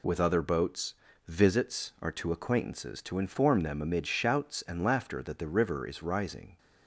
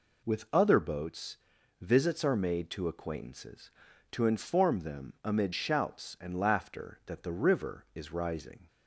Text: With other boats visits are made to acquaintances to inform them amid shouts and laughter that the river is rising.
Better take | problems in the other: second | pauses between "boats" and "visits"; slight; at 0.9 s; 0.34 s long; also in the second // skips "made"; at 2.1 s

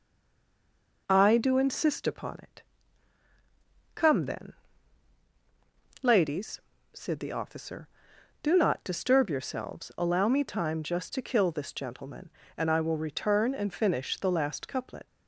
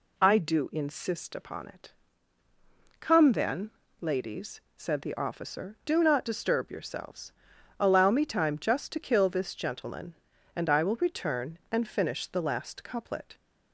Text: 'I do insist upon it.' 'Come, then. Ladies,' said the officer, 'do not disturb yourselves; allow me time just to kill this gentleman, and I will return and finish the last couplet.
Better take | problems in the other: second | stays silent before the first word; until 1.0 s; 1.0 s long

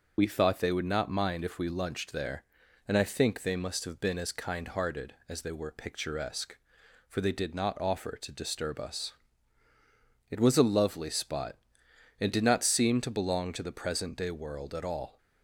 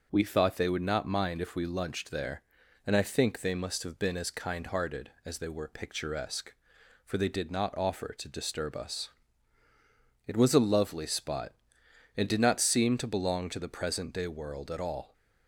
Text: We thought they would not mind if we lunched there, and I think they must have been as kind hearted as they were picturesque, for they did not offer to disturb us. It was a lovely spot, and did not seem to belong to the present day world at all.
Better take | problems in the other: second | loses the start of "We"; at 0.1 s; 35 ms

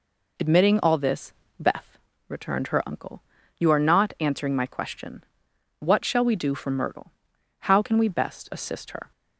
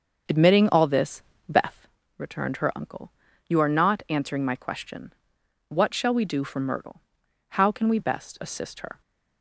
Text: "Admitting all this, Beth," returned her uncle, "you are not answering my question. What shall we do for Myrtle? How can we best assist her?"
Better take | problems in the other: first | starts louder than the rest; until 1.9 s; 6.5 dB

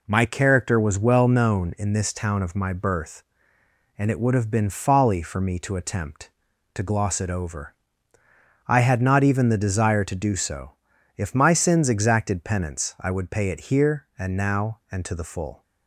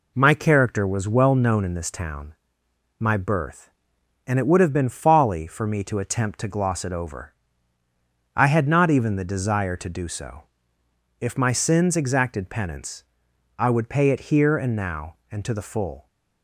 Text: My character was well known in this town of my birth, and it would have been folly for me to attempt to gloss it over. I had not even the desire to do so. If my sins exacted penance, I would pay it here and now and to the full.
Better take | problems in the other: first | skips "of"; at 2.6 s

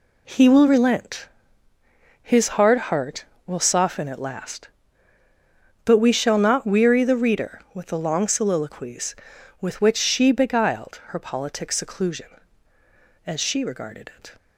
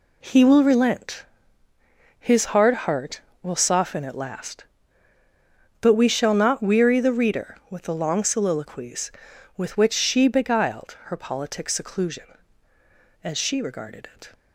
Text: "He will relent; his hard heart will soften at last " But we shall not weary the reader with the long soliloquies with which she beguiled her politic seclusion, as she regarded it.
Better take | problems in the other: neither | none

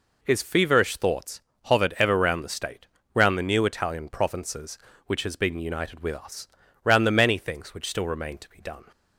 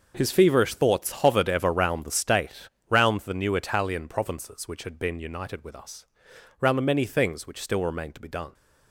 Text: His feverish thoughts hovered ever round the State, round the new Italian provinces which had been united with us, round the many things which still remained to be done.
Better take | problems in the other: second | pauses between "thoughts" and "hovered"; slight; at 1.4 s; 0.24 s long // says "has" for "had"; at 5.2 s

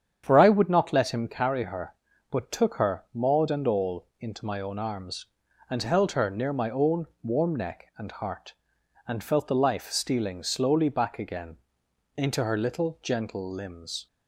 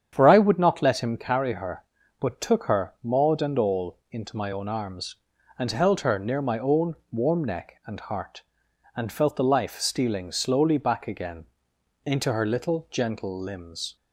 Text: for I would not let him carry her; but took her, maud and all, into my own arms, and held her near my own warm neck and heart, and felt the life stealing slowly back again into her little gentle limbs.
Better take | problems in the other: neither | starts louder than the rest; strong; the same in both // pauses between "own" and "warm"; slight; the same in both // pauses between "again" and "into"; noticeable; the same in both

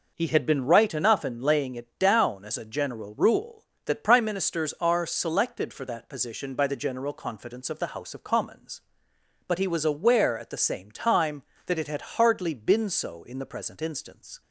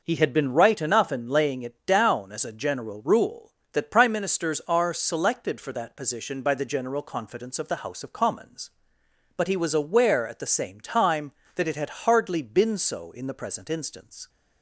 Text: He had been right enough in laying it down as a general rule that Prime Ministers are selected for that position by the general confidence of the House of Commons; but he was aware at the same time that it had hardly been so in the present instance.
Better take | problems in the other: neither | none

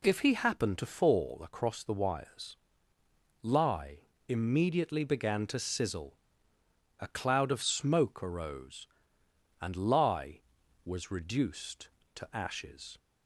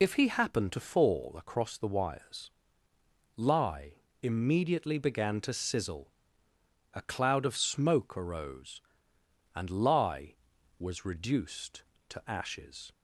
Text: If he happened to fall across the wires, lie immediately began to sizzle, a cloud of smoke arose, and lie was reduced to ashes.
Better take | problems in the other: first | loses the start of "If"; at 0.0 s; 45 ms // pauses between "lie" and "immediately"; slight; at 3.9 s; 0.28 s long; slight in the first

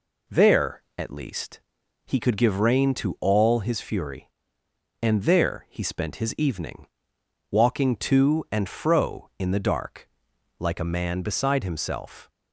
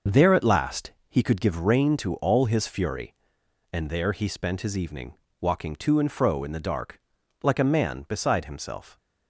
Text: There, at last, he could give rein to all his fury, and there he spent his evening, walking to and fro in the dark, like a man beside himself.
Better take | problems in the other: second | says "least" for "last"; at 1.1 s

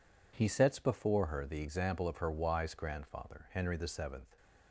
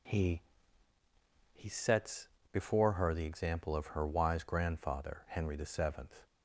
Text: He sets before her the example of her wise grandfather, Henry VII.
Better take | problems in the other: first | says "He" twice; at 1.5 s // pauses between "sets" and "before"; slight; at 2.2 s; 0.24 s long

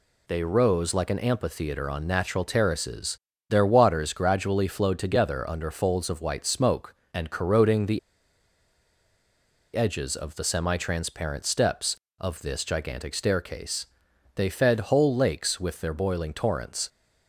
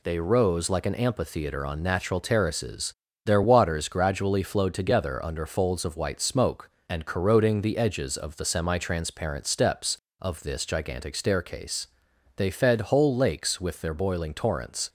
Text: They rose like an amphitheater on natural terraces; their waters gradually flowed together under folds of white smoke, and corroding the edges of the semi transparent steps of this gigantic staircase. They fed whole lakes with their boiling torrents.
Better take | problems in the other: second | pauses between "the" and "edges"; strong; at 7.9 s; 1.7 s long

